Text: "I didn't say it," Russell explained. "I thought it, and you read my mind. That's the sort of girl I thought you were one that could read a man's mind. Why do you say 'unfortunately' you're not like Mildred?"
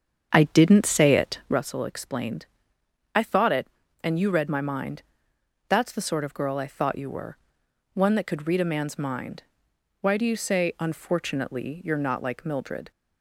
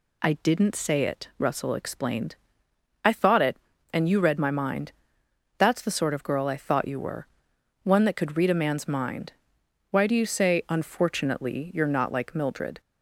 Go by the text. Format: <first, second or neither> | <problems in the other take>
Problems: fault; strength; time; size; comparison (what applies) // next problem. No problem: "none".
second | starts louder than the rest; strong; until 1.6 s; 7.5 dB // pauses between "were" and "one"; noticeable; at 7.3 s; 0.58 s long; noticeable in the second